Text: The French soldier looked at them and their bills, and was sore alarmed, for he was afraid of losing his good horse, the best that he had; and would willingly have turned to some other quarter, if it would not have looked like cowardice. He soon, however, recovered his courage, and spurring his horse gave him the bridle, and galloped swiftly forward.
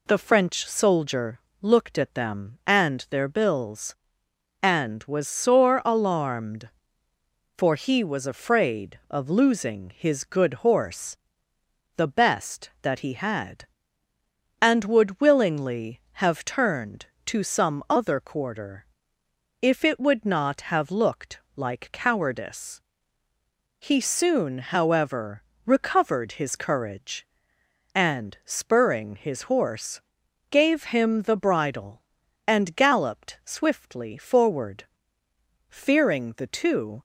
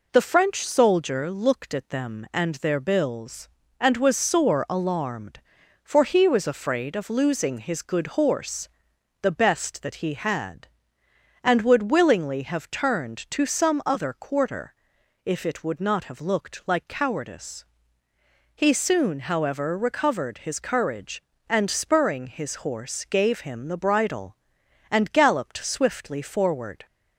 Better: second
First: pauses between "soldier" and "looked"; slight; at 1.4 s; 0.20 s long // pauses between "looked" and "like"; slight; at 21.3 s; 0.18 s long // pauses between "horse" and "gave"; noticeable; at 30.0 s; 0.50 s long // goes on to say "Fearing the two"; from 35.6 s on; 1.3 s long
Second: none

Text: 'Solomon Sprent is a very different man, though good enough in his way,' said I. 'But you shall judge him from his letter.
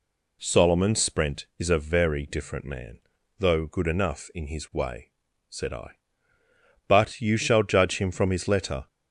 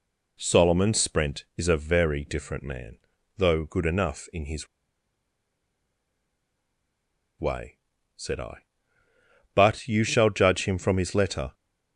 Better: first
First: none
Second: pauses between "his" and "way"; strong; at 4.6 s; 2.7 s long

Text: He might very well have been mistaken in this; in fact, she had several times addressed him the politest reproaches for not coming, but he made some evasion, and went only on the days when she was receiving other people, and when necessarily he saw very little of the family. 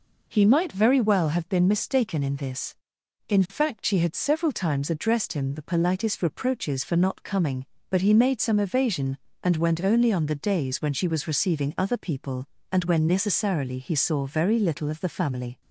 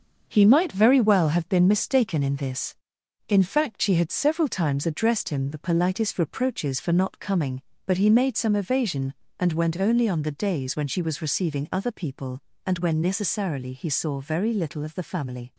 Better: first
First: none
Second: gets quieter; noticeable; throughout; 6 dB

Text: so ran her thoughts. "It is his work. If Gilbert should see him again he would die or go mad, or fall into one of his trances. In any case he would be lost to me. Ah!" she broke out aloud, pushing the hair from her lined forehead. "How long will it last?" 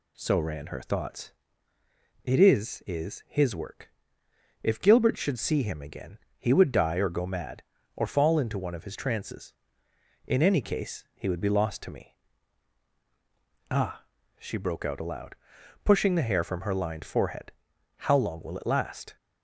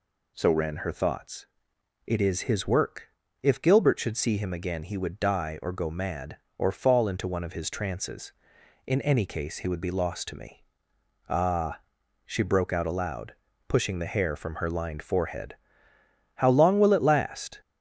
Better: second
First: says "is" twice; at 2.8 s // pauses between "again" and "he"; slight; at 6.1 s; 0.22 s long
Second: none

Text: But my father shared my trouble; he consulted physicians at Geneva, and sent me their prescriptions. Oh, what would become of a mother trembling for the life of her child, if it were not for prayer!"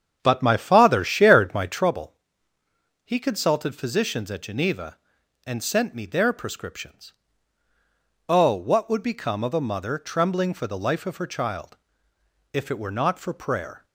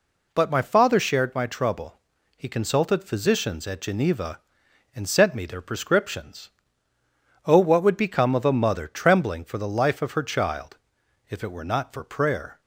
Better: second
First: starts louder than the rest; strong; until 1.9 s; 8 dB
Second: none

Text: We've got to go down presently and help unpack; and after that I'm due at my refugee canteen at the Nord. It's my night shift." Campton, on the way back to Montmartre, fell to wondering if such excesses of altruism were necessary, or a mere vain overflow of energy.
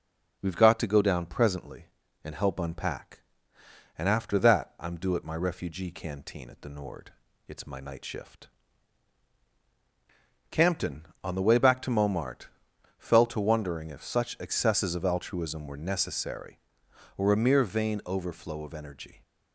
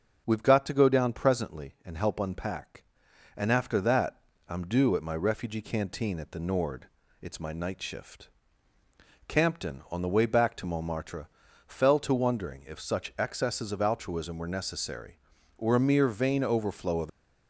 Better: first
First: none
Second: starts louder than the rest; until 1.2 s; 6.5 dB // pauses between "that" and "I'm"; slight; at 4.2 s; 0.30 s long // stops before "energy"; at 17.0 s

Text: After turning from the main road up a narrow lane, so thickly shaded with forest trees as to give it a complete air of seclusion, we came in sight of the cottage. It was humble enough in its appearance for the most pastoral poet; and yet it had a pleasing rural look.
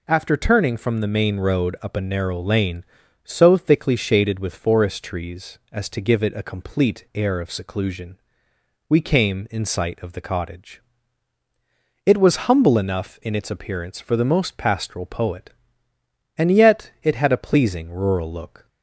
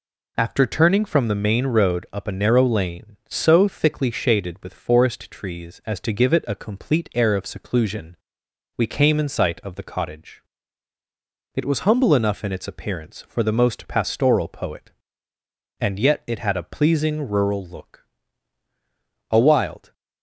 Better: first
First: none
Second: goes on to say "A wild"; noticeable; from 19.3 s on; 0.62 s long

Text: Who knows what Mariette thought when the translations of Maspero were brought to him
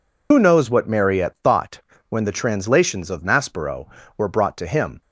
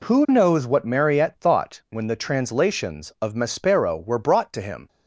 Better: second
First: loses the start of "Who"; at 0.3 s; 60 ms // pauses between "thought" and "when"; slight; at 1.8 s; 0.28 s long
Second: none

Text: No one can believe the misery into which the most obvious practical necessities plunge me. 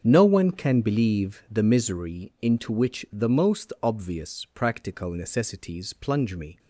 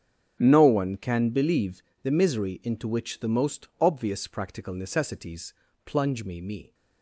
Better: first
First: starts louder than the rest; strong; until 1.0 s; 7.5 dB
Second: starts louder than the rest; strong; until 1.4 s; 7.5 dB // pauses between "believe" and "the"; slight; at 1.8 s; 0.22 s long // pauses between "necessities" and "plunge"; slight; at 5.5 s; 0.32 s long // says "me" twice; at 6.3 s

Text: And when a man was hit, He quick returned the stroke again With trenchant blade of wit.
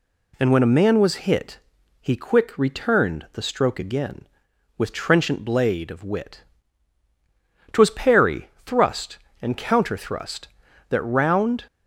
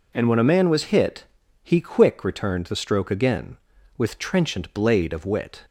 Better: second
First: goes on to say "Twas parry thrust and counter thrust That round"; strong; from 7.7 s on; 3.9 s long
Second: none

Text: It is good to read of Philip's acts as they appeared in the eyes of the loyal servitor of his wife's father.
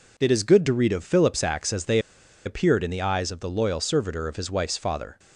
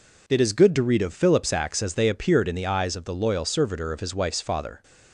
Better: second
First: pauses between "they" and "appeared"; noticeable; at 1.9 s; 0.46 s long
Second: none

